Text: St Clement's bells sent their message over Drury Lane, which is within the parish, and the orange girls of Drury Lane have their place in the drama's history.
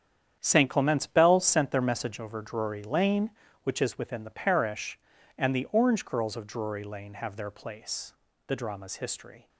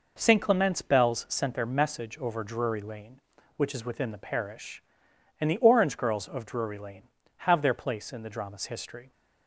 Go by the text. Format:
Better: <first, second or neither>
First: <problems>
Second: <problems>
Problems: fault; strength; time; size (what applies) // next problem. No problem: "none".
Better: second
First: starts louder than the rest; strong; until 1.4 s; 9 dB // skips "in"; at 8.2 s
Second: none